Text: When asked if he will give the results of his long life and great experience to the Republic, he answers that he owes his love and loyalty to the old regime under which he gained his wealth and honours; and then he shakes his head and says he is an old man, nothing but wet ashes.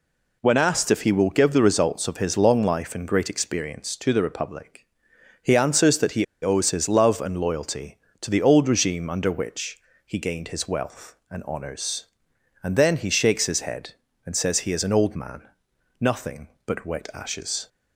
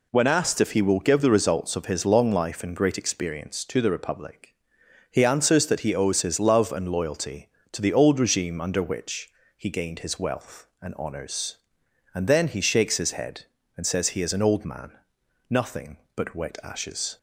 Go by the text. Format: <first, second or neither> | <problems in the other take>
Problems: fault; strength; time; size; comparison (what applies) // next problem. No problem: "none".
second | pauses between "he" and "owes"; slight; at 6.2 s; 0.19 s long // pauses between "which" and "he"; slight; at 9.7 s; 0.28 s long; slight in the second